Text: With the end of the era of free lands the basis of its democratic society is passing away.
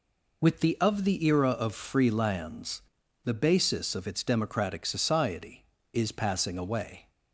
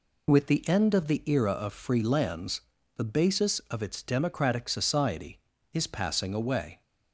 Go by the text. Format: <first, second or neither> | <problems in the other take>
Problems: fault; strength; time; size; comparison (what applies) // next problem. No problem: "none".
second | skips "end"; at 0.7 s // pauses between "lands" and "the"; at 2.8 s; 0.44 s long; slight in the second